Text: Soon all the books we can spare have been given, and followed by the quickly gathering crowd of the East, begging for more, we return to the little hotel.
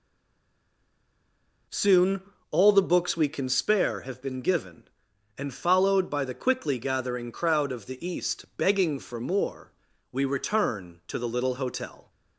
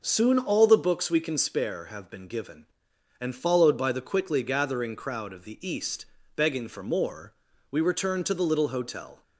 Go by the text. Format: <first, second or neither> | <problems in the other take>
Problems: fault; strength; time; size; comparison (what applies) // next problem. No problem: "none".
second | stays silent before the first word; noticeable; until 1.6 s; 1.6 s long // pauses between "Soon" and "all"; slight; at 2.2 s; 0.28 s long